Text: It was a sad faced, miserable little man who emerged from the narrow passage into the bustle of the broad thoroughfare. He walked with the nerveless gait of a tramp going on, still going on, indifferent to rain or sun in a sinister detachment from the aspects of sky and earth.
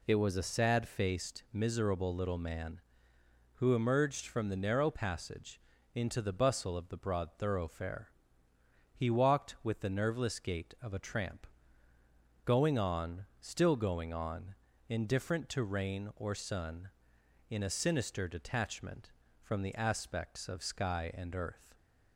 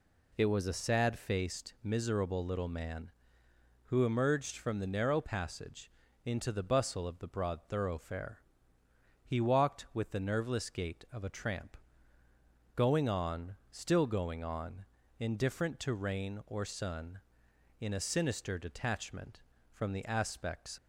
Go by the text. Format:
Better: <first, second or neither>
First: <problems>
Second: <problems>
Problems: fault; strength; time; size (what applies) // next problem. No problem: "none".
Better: first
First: pauses between "passage" and "into"; slight; at 5.6 s; 0.34 s long // pauses between "tramp" and "going"; noticeable; at 11.4 s; 0.98 s long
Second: pauses between "passage" and "into"; slight; at 5.9 s; 0.34 s long // pauses between "tramp" and "going"; noticeable; at 11.7 s; 0.98 s long // stops before "of sky and earth"; at 20.7 s